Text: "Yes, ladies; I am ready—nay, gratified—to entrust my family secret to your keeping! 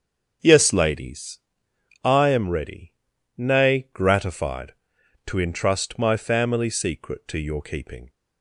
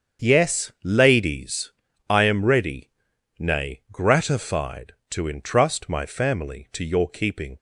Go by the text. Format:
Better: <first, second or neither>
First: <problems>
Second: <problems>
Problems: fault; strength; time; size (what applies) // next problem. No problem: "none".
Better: first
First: starts louder than the rest; until 2.0 s; 7 dB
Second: starts louder than the rest; strong; until 1.3 s; 7.5 dB // skips "secret"; at 6.7 s